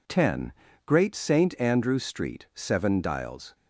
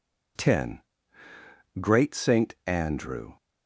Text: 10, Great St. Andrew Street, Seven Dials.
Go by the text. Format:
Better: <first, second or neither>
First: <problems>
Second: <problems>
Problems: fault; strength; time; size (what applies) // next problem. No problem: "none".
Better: first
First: none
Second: stops before "Street Seven Dials"; at 3.3 s